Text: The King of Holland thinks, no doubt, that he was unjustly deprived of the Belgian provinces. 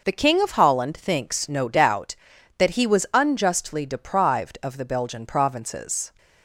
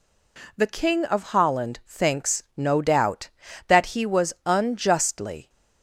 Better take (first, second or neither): first